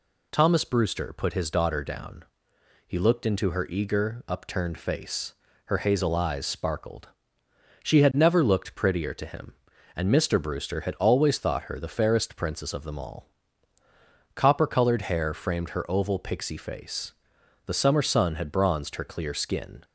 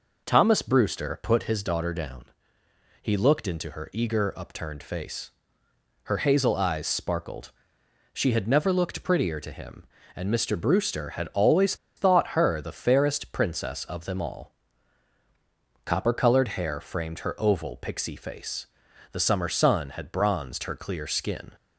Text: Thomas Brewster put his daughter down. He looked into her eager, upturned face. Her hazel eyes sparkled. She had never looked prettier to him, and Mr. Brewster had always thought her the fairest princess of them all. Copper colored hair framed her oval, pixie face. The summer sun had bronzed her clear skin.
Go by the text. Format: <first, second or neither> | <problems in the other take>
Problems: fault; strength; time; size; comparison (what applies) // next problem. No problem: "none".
first | pauses between "always" and "thought"; slight; at 11.7 s; 0.21 s long